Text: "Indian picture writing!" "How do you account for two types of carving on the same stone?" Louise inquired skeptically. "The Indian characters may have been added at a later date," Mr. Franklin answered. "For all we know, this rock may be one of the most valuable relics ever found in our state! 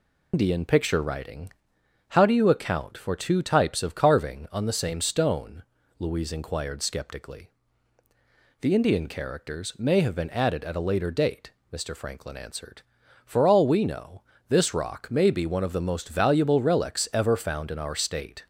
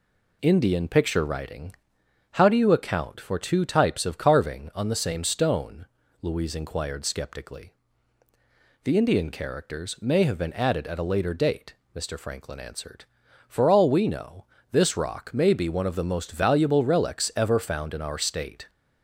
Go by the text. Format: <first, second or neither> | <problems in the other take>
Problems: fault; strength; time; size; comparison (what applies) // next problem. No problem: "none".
second | loses the start of "Indian"; at 0.3 s; 155 ms